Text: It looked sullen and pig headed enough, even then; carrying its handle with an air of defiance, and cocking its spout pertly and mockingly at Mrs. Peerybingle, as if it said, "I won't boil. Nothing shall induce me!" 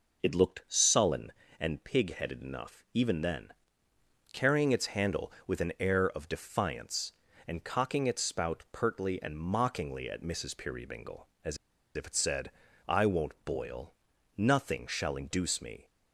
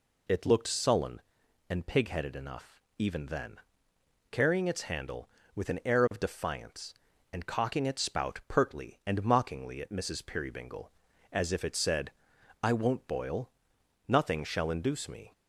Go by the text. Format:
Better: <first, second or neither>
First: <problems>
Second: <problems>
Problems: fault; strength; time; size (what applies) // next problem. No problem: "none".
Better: second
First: pauses between "as" and "if"; at 11.5 s; 0.40 s long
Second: none